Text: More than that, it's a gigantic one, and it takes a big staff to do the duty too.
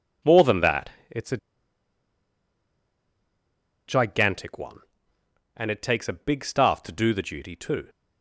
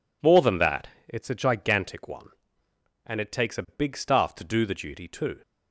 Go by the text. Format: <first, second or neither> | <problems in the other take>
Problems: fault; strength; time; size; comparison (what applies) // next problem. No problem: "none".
second | pauses between "a" and "gigantic"; strong; at 1.3 s; 2.5 s long